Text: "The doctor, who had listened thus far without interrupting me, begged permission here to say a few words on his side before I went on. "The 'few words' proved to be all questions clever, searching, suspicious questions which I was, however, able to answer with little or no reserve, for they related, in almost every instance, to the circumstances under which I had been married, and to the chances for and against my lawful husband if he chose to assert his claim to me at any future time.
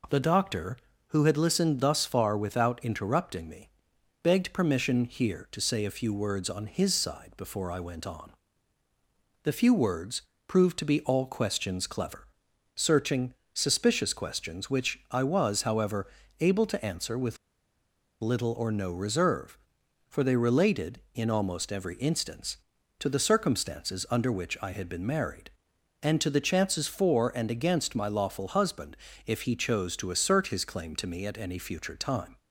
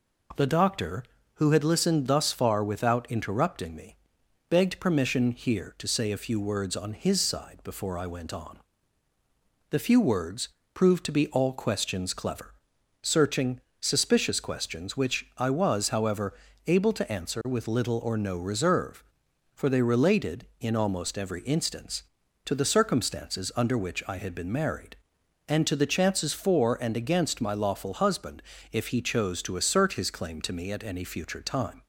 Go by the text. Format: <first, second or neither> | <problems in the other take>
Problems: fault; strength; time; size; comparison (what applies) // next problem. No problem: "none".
second | pauses between "words" and "proved"; slight; at 10.2 s; 0.24 s long; slight in the second // pauses between "with" and "little"; noticeable; at 17.3 s; 0.85 s long // pauses between "husband" and "if"; slight; at 28.9 s; 0.30 s long; slight in the second